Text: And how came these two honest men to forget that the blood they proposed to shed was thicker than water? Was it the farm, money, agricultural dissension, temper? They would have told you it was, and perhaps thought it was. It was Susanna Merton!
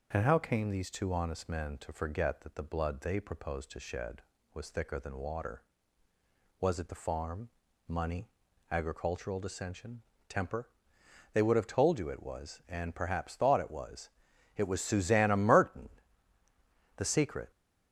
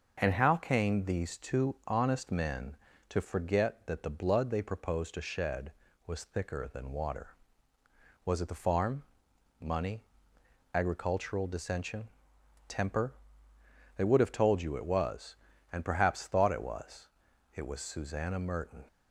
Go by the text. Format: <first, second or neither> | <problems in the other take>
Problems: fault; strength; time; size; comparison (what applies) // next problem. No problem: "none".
second | goes on to say "The secret"; from 16.9 s on; 0.54 s long